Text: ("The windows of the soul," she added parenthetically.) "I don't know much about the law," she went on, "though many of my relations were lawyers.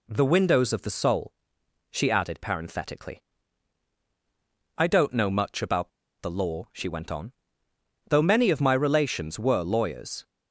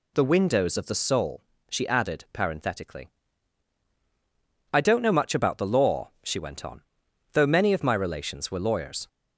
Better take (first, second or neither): second